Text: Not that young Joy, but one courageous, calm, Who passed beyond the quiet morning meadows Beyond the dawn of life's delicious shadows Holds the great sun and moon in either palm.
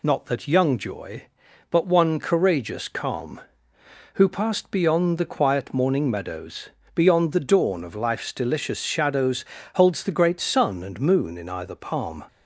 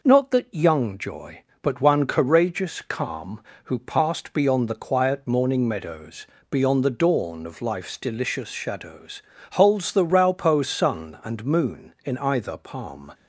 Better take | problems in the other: first | pauses between "meadows" and "Beyond"; slight; at 6.2 s; 0.24 s long; slight in the first // pauses between "shadows" and "Holds"; slight; at 9.2 s; 0.32 s long; slight in the first // says "raupo" for "great"; at 10.0 s

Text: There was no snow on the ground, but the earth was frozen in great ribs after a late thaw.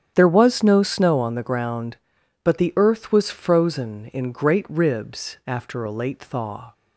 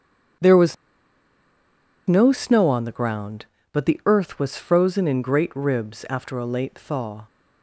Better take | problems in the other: first | starts louder than the rest; strong; until 2.7 s; 8.5 dB; strong in the first // pauses between "was" and "no"; strong; at 0.7 s; 1.3 s long

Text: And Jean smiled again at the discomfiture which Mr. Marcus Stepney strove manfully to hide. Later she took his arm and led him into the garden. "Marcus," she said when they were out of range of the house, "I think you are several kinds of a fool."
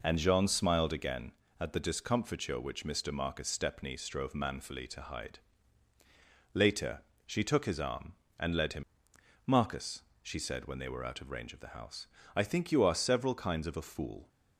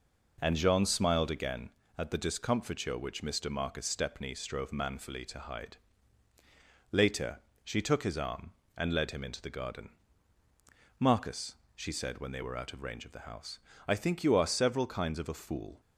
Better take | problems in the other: second | pauses between "Later" and "she"; slight; at 7.0 s; 0.24 s long; slight in the second // skips "into the garden"; at 9.1 s

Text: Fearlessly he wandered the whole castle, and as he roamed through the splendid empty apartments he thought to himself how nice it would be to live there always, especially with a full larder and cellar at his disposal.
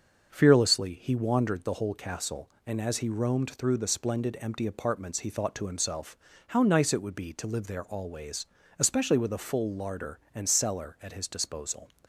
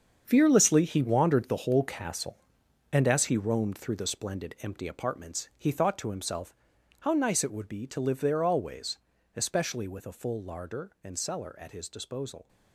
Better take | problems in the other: first | gets quieter; strong; throughout; 11 dB // starts louder than the rest; strong; until 1.2 s; 7 dB; also in the first // pauses between "himself" and "how"; noticeable; at 6.5 s; 0.48 s long; slight in the first

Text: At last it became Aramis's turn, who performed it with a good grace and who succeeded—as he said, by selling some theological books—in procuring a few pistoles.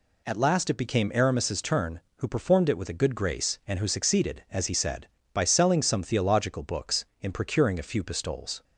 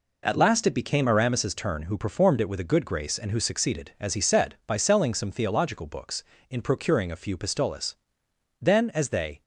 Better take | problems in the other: first | goes on to say "Then as they"; noticeable; from 8.6 s on; 0.82 s long

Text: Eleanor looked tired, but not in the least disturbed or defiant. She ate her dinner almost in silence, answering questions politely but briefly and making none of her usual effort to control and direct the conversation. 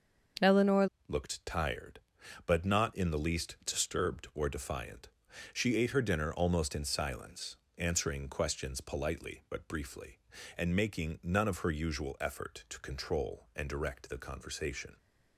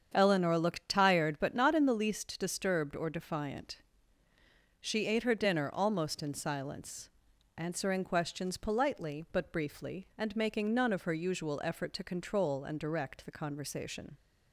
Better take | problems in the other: second | starts louder than the rest; until 1.6 s; 6.5 dB; strong in the second // changes voice at "looked"; from 1.0 s on; 13.9 s long

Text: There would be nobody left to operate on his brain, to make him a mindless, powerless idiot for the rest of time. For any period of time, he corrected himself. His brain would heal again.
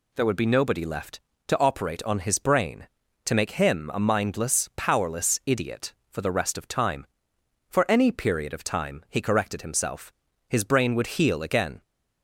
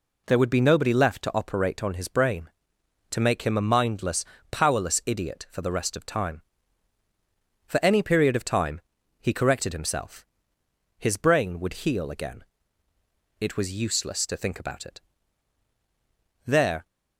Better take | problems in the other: first | goes on to say "It was useless to think about it There"; strong; from 13.3 s on; 3.4 s long

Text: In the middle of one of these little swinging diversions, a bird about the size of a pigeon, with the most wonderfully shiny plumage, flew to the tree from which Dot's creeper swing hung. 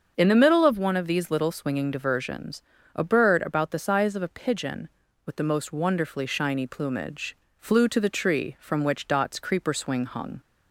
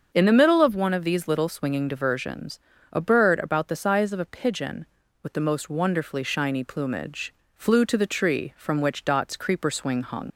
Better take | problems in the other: first | starts louder than the rest; until 1.1 s; 7 dB; also in the first // leaves "hung" unfinished; at 10.3 s; 70 ms

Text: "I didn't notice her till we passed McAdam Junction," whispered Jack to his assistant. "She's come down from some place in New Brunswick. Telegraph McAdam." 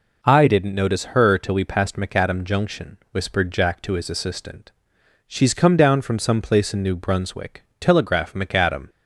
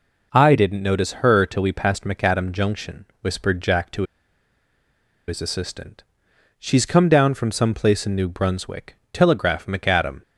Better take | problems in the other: first | pauses between "to" and "his"; at 4.0 s; 1.2 s long

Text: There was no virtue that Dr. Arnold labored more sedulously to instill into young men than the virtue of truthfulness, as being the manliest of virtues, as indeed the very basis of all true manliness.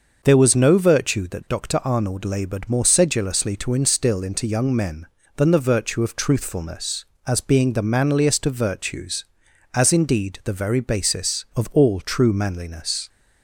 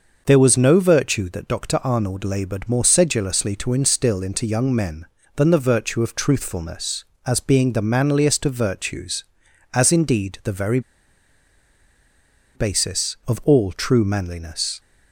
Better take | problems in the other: first | pauses between "very" and "basis"; strong; at 10.7 s; 1.7 s long

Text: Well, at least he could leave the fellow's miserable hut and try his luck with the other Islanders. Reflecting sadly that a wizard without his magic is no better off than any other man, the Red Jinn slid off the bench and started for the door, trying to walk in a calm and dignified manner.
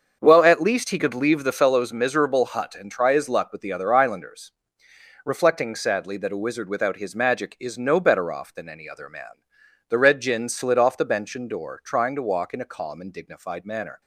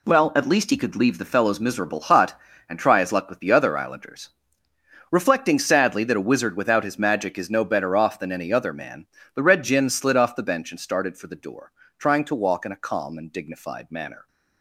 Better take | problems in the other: second | starts louder than the rest; until 1.2 s; 6.5 dB // skips "started for the"; at 11.4 s

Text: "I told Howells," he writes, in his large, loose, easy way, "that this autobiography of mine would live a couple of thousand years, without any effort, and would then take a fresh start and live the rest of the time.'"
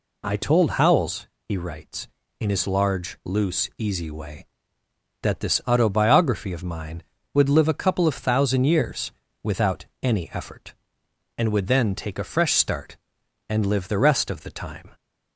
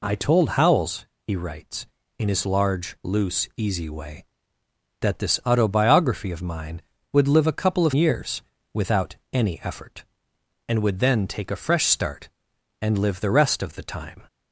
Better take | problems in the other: first | skips "thousand"; at 7.9 s // pauses between "without" and "any"; slight; at 9.1 s; 0.16 s long; slight in the first

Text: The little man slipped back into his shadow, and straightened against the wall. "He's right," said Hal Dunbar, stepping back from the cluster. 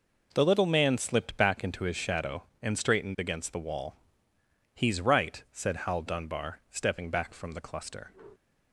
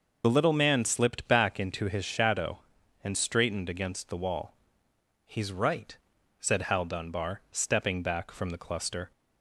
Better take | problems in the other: first | loses the start of "The"; at 0.2 s; 40 ms

